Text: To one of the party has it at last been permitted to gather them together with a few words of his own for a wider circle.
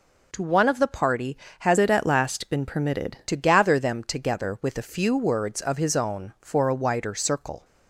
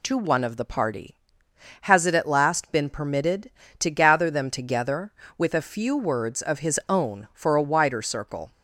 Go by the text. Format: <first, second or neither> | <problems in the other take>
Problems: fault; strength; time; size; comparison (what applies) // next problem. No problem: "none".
second | changes voice from "it" to "permitted"; from 1.7 to 3.1 s; 1.4 s long